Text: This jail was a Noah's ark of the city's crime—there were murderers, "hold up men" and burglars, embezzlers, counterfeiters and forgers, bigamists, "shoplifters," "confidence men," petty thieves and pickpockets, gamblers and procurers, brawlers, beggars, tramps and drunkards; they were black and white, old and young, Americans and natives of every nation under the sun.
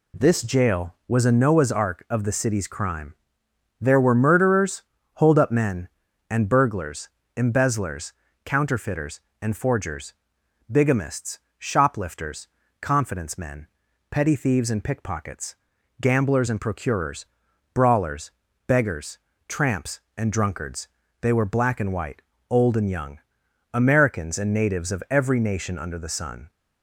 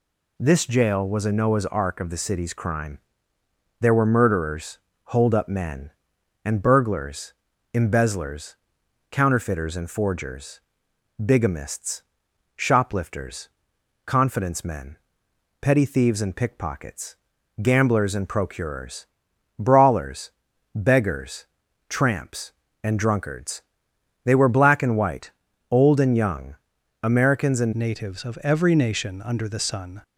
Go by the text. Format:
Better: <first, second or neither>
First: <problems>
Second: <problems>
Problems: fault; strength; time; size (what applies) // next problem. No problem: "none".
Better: first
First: none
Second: changes voice at "natives"; from 27.7 s on; 2.3 s long